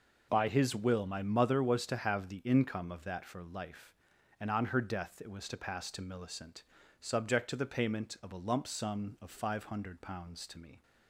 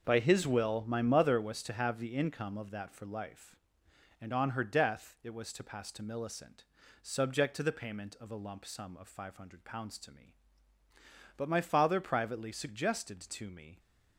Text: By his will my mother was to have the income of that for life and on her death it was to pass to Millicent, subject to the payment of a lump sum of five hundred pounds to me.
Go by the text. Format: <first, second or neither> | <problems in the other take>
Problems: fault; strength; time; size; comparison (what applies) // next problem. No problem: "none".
first | goes on to say "But my father privately suggested to me"; strong; from 11.3 s on; 2.4 s long